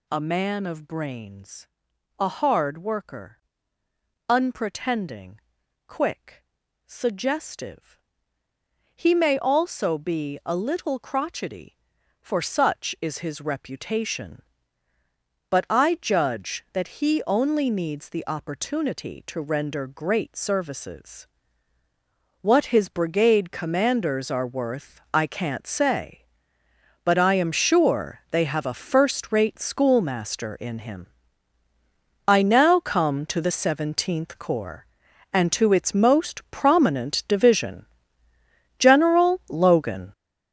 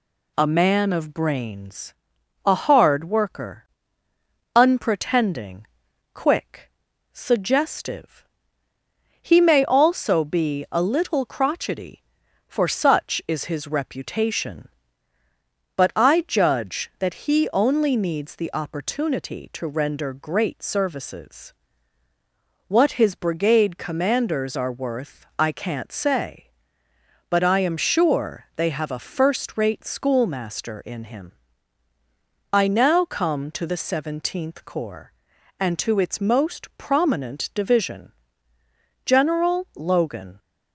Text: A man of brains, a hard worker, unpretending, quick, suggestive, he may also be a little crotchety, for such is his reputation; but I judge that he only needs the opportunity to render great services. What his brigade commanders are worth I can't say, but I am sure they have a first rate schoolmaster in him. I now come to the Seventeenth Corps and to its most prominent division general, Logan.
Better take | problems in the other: second | gets louder; strong; throughout; 10.5 dB // pauses between "division" and "general"; noticeable; at 37.8 s; 0.94 s long; noticeable in the second

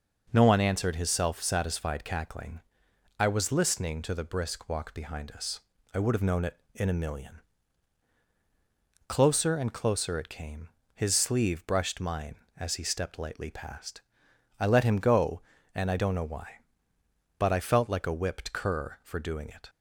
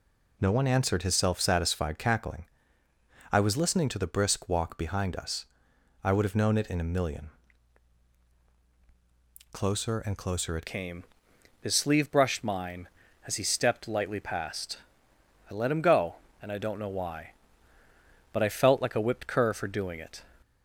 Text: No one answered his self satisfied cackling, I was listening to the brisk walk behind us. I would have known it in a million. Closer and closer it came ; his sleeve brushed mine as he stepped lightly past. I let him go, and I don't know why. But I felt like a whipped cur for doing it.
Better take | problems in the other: first | changes voice at "came"; from 10.6 s on; 9.6 s long

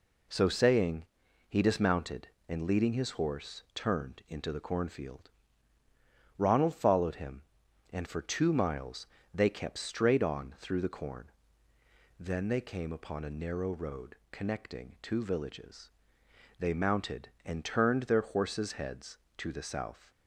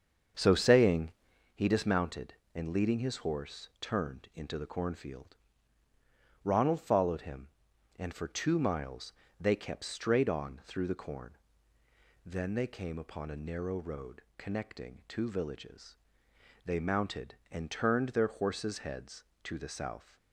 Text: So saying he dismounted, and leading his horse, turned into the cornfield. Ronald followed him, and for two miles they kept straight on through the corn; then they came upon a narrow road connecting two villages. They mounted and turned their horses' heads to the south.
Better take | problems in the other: first | starts louder than the rest; until 1.5 s; 7 dB // pauses between "saying" and "he"; at 1.1 s; 0.44 s long; also in the first // pauses between "miles" and "they"; slight; at 9.1 s; 0.26 s long; slight in the first

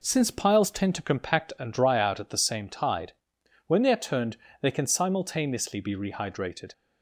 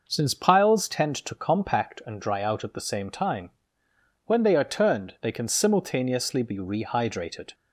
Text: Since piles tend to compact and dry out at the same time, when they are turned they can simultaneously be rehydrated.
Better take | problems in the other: second | says "tide" for "time"; at 2.6 s // pauses between "turned" and "they"; slight; at 4.3 s; 0.24 s long

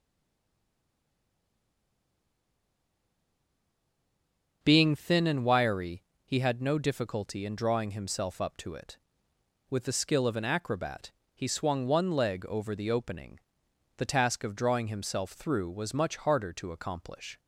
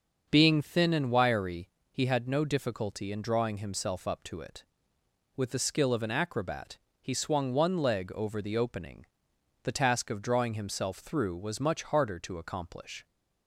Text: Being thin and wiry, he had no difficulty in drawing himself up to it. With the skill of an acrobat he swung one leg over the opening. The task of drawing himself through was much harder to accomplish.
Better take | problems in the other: second | stays silent before the first word; strong; until 4.6 s; 4.6 s long // starts louder than the rest; until 5.6 s; 6.5 dB; also in the second // pauses between "acrobat" and "he"; slight; at 11.1 s; 0.22 s long; slight in the second

